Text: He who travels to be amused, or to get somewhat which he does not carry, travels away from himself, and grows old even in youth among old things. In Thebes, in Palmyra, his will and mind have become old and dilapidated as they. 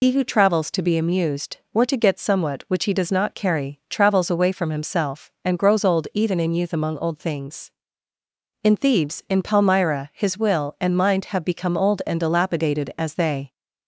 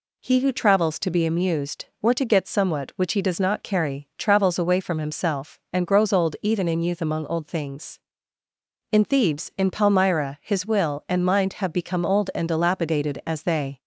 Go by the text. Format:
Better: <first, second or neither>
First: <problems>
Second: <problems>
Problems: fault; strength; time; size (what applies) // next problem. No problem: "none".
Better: second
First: loses the start of "He"; at 0.0 s; 95 ms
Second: none